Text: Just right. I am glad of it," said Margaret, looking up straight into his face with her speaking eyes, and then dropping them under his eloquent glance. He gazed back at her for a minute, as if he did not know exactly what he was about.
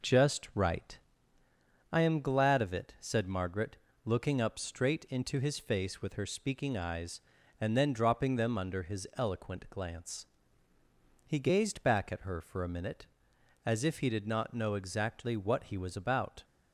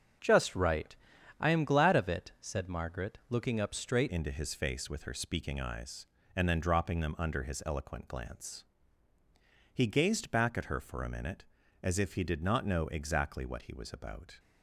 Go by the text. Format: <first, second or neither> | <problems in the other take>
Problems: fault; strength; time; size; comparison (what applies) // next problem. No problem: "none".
first | starts louder than the rest; strong; until 1.6 s; 7 dB // changes voice at "into"; from 4.0 s on; 10.3 s long